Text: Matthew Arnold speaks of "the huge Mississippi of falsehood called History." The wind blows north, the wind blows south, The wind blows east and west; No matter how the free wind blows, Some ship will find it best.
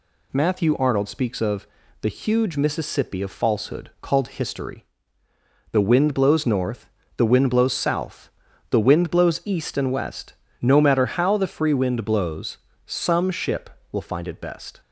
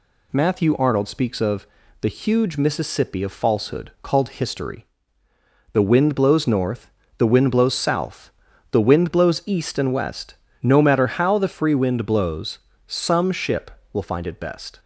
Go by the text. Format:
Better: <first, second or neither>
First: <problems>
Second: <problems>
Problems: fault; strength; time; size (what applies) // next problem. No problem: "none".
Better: neither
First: pauses between "of" and "the"; slight; at 1.6 s; 0.36 s long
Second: pauses between "of" and "the"; slight; at 1.6 s; 0.36 s long